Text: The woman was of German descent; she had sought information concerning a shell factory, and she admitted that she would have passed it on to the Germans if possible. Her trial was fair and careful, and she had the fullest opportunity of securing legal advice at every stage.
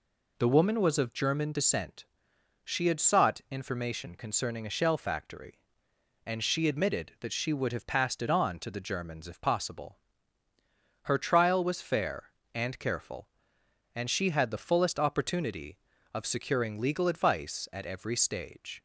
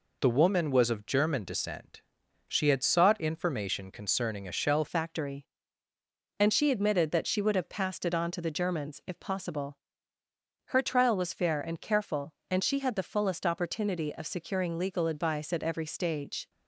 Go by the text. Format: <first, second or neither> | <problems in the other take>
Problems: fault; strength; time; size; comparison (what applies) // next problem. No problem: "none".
first | changes voice at "factory"; from 4.8 s on; 11.6 s long